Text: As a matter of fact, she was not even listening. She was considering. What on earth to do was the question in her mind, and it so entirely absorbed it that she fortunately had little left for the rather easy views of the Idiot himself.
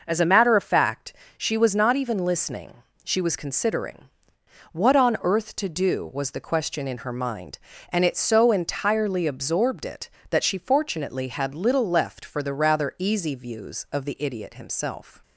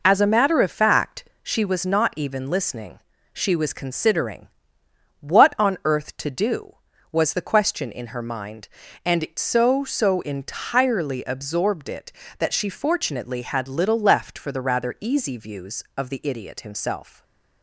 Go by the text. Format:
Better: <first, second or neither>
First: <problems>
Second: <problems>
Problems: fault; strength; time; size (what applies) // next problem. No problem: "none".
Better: first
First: none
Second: says "so" twice; at 9.8 s // stays silent after the last word; slight; from 17.0 s on; 0.6 s long